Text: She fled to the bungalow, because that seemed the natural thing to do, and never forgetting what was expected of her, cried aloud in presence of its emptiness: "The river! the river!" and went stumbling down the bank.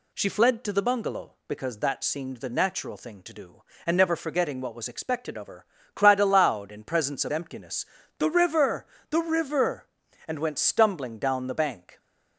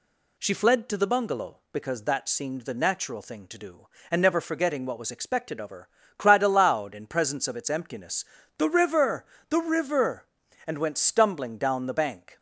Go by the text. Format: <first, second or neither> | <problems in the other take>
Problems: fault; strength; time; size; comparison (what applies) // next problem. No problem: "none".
second | skips "its"; at 7.3 s